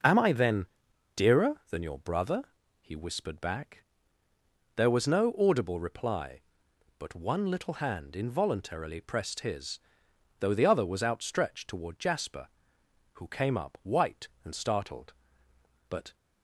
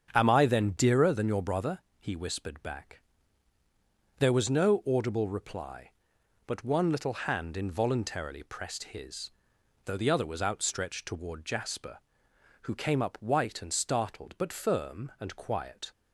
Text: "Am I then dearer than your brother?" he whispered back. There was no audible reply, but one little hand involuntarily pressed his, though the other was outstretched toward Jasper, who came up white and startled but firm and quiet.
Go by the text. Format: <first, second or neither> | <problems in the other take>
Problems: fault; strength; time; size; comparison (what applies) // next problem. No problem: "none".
second | starts louder than the rest; noticeable; until 1.5 s; 6 dB; strong in the second // pauses between "then" and "dearer"; noticeable; at 0.6 s; 0.48 s long // stops before "firm and quiet"; at 16.1 s